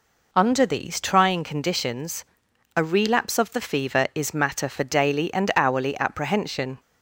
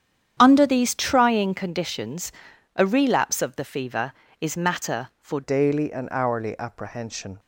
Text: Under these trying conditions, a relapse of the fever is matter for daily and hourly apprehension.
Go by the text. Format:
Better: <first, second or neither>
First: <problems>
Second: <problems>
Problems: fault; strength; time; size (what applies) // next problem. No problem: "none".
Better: first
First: none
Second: starts louder than the rest; strong; until 1.3 s; 9.5 dB // changes voice at "daily"; from 5.4 s on; 1.9 s long